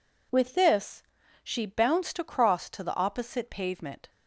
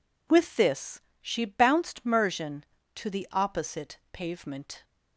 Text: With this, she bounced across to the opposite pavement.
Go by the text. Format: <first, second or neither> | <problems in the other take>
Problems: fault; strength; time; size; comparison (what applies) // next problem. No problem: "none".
first | says "mersion" for "across"; at 2.0 s